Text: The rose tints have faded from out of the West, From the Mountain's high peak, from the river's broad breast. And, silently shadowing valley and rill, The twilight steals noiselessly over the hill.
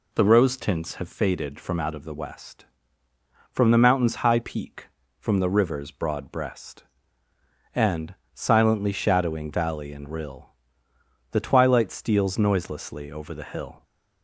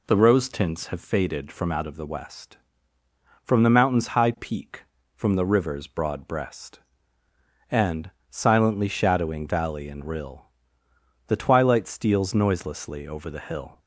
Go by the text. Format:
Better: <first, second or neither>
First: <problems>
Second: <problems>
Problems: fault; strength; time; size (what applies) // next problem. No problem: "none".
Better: neither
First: none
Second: none